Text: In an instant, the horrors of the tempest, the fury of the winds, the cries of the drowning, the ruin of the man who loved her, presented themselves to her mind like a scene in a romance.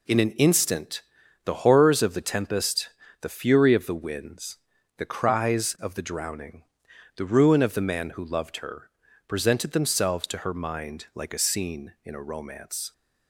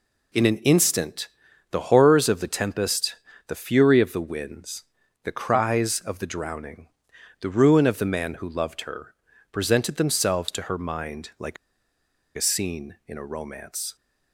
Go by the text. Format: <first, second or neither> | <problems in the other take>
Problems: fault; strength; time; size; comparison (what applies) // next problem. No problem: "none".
first | pauses between "like" and "a"; noticeable; at 11.5 s; 0.80 s long